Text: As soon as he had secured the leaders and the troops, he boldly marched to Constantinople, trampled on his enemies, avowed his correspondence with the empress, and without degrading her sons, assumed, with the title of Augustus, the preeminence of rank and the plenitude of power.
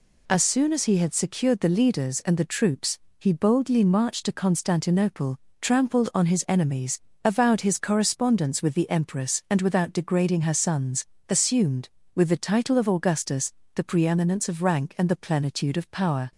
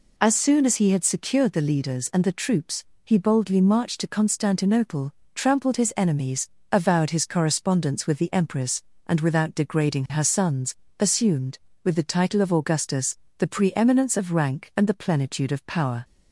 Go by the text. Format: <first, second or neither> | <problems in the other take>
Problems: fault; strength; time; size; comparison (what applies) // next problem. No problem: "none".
first | skips "on"; at 5.7 s